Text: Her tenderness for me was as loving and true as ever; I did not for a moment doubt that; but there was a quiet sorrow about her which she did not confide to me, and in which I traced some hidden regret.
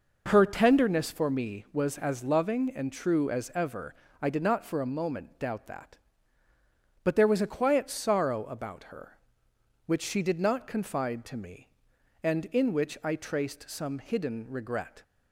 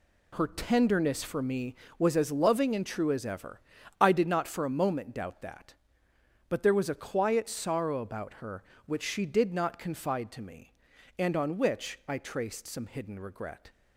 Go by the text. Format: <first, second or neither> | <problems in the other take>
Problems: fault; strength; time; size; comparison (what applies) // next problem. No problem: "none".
first | says "on" for "in"; at 11.3 s